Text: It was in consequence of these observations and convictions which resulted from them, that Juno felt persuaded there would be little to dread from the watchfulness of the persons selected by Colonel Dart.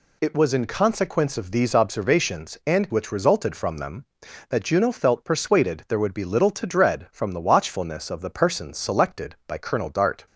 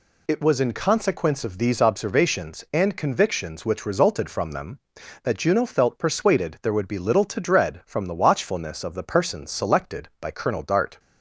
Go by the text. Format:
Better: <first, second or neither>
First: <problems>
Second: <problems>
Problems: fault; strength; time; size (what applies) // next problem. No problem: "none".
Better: second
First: skips "convictions"; at 2.9 s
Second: none